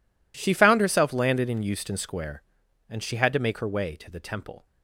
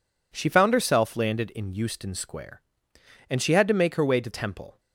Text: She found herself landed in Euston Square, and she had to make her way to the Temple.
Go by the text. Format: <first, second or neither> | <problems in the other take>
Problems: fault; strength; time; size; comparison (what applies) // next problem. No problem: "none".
first | skips "the"; at 4.3 s